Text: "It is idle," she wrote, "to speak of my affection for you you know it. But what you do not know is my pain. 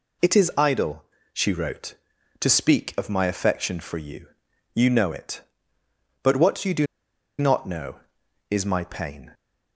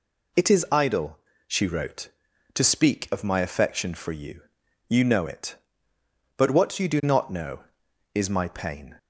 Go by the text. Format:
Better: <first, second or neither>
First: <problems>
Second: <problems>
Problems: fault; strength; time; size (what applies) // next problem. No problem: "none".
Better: second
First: pauses between "you" and "you"; noticeable; at 4.2 s; 0.48 s long // pauses between "do" and "not"; noticeable; at 6.8 s; 0.53 s long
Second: pauses between "you" and "you"; noticeable; at 4.4 s; 0.48 s long